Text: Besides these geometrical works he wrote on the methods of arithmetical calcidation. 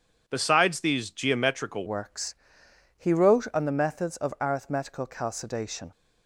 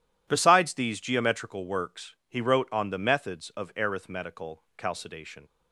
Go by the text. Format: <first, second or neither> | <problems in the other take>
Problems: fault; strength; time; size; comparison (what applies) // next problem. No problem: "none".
second | changes voice at "works"; from 1.8 s on; 4.1 s long // pauses between "works" and "he"; noticeable; at 2.3 s; 0.62 s long